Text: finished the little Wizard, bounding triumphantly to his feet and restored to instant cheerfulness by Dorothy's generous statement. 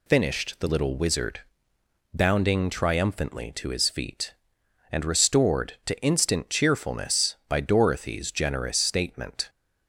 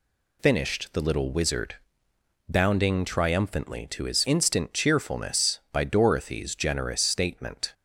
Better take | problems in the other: first | skips "feet and restored to"; at 4.2 s

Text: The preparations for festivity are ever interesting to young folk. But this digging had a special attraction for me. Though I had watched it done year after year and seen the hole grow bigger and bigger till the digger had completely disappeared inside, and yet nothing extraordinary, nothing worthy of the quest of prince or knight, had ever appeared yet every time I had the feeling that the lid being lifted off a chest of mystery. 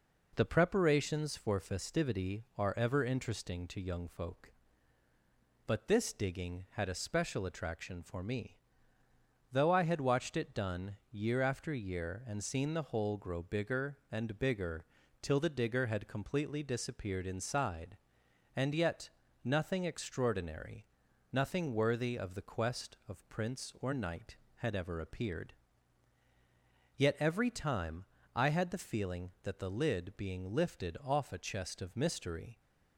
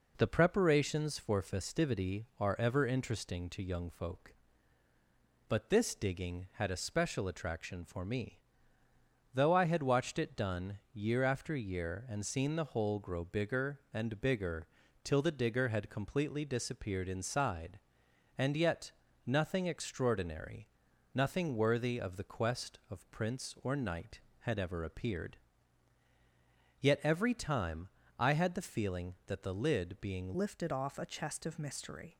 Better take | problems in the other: first | pauses between "done" and "year"; slight; at 10.7 s; 0.16 s long; slight in the first // pauses between "bigger" and "till"; at 14.6 s; 0.38 s long; also in the first // pauses between "yet" and "nothing"; slight; at 18.9 s; 0.34 s long; slight in the first // pauses between "appeared" and "yet"; strong; at 25.3 s; 1.4 s long; strong in the first // pauses between "time" and "I"; slight; at 27.8 s; 0.28 s long; slight in the first // changes voice at "lifted"; from 30.3 s on; 1.8 s long

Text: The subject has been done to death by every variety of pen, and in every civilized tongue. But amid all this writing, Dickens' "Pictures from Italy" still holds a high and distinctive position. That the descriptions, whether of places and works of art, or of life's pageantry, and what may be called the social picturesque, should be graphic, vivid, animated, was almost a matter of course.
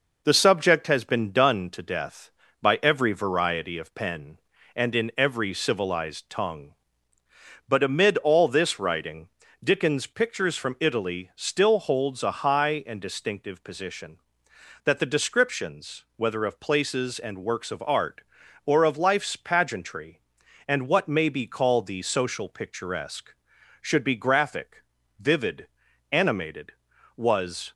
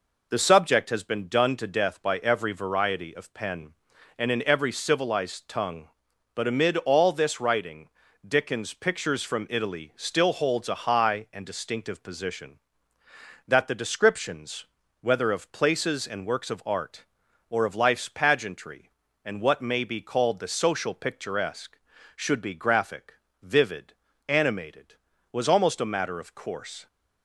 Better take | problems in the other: second | stops before "almost a matter of course"; at 27.7 s

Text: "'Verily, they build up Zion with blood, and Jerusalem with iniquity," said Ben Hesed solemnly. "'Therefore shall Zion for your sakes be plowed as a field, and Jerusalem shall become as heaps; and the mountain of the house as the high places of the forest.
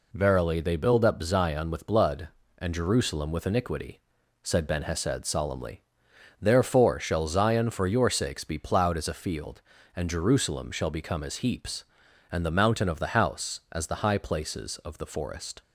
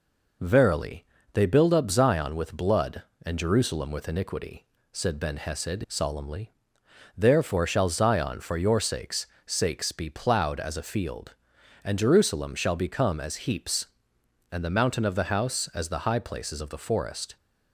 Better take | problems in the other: first | says "sakes" twice; at 9.4 s

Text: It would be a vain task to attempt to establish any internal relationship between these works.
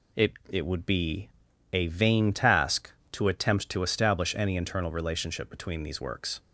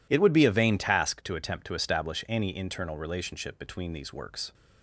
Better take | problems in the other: second | says "It" twice; at 0.4 s // pauses between "be" and "a"; at 1.2 s; 0.42 s long

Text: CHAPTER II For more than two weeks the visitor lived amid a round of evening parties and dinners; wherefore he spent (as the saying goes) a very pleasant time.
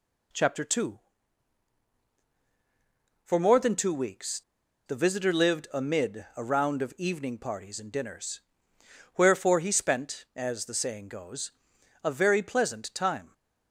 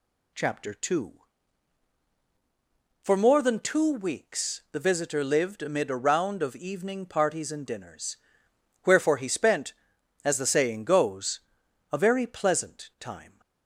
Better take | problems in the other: second | pauses between "weeks" and "the"; at 4.4 s; 0.45 s long

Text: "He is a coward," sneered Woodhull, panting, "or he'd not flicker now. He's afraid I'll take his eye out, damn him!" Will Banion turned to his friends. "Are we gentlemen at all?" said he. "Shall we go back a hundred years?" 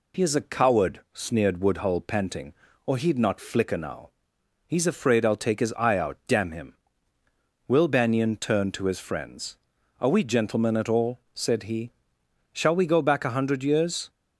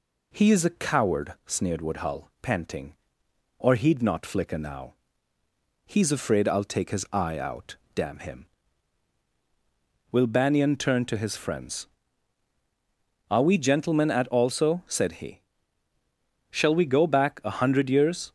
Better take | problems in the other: first | says "also" for "all"; at 14.2 s

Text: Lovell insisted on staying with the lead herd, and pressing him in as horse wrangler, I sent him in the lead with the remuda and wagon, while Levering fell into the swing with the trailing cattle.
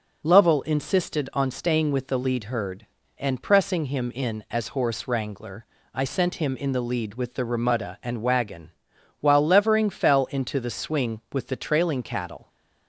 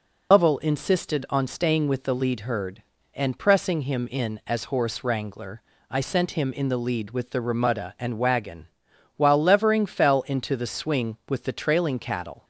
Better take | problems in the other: first | loses the start of "Lovell"; at 0.3 s; 105 ms

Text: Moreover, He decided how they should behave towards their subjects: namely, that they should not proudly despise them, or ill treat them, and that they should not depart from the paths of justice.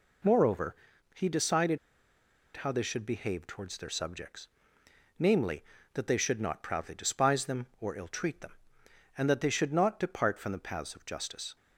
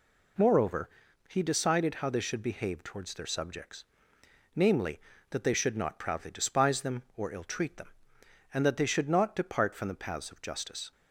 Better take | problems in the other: second | pauses between "decided" and "how"; noticeable; at 1.7 s; 0.79 s long

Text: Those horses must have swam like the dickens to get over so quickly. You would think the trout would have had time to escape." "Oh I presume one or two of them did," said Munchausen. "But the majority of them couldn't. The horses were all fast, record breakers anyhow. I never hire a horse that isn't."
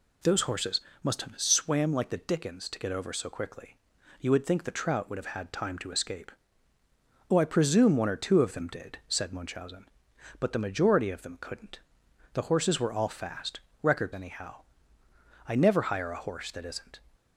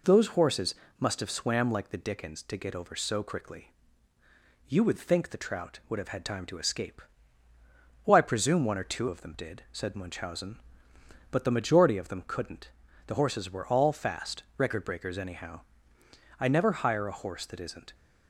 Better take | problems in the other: second | pauses between "horses" and "must"; slight; at 0.8 s; 0.22 s long; slight in the second // skips "breakers"; at 14.1 s

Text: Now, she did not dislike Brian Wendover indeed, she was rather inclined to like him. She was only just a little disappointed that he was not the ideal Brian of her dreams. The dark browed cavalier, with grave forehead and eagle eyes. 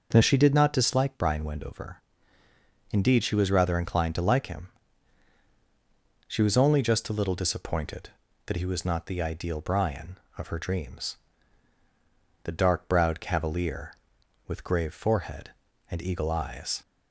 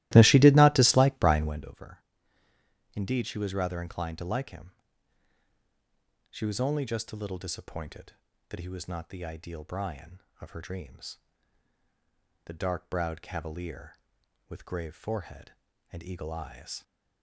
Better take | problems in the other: first | starts louder than the rest; strong; until 1.7 s; 17 dB // pauses between "Wendover" and "indeed"; noticeable; at 1.9 s; 0.96 s long; noticeable in the first

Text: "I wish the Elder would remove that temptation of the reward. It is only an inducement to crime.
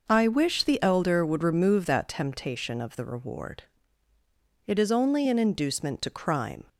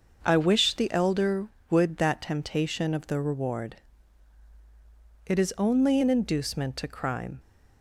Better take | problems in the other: first | starts louder than the rest; noticeable; until 1.2 s; 6 dB // skips "remove"; at 1.9 s

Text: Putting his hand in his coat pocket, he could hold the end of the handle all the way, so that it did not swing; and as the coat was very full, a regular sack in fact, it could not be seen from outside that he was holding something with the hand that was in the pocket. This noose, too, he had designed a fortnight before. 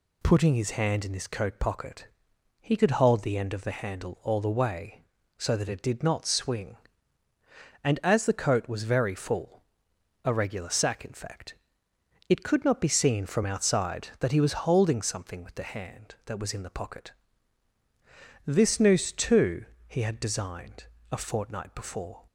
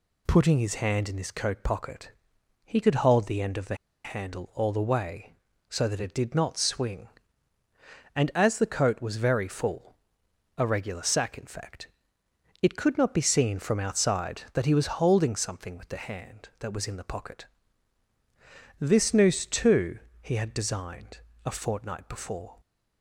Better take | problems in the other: first | pauses between "the" and "handle"; slight; at 3.7 s; 0.30 s long // pauses between "designed" and "a"; slight; at 21.1 s; 0.26 s long; slight in the first

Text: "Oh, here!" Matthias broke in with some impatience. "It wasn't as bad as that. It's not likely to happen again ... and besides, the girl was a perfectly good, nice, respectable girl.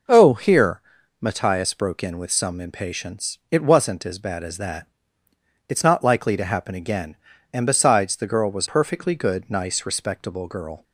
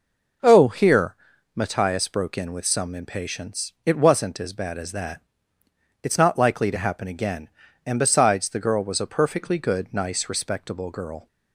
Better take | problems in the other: second | skips "a"; at 8.6 s

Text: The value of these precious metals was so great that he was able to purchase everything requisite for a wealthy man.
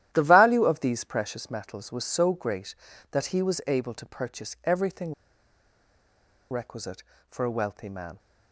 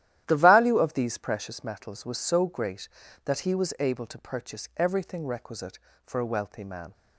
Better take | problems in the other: second | starts louder than the rest; strong; until 1.1 s; 12.5 dB; strong in the second // pauses between "everything" and "requisite"; strong; at 5.1 s; 1.3 s long

